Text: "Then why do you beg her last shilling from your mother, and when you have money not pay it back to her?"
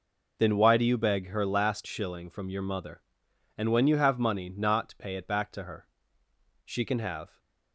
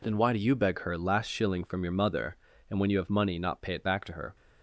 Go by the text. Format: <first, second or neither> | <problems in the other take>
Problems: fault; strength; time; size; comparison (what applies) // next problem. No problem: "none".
second | goes on to say "She can have"; noticeable; from 6.6 s on; 0.74 s long